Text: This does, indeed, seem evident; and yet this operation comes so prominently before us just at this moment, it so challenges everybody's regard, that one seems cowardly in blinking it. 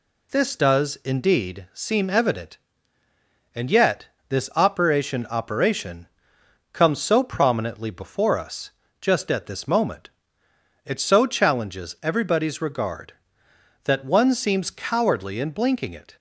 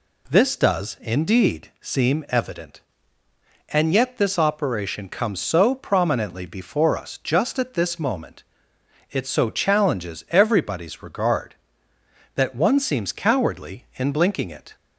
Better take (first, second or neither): second